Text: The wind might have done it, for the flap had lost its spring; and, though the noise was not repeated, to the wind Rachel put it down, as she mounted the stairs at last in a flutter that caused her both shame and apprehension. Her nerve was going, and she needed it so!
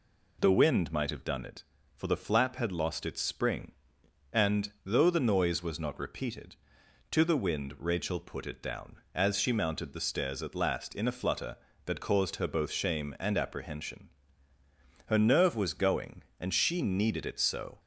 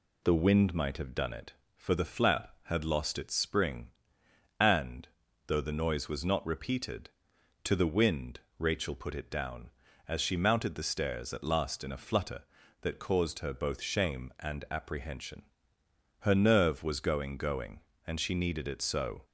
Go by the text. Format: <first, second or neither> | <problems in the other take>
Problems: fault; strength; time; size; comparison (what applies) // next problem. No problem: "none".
first | pauses between "wind" and "Rachel"; slight; at 8.3 s; 0.18 s long // says "going" twice; at 17.3 s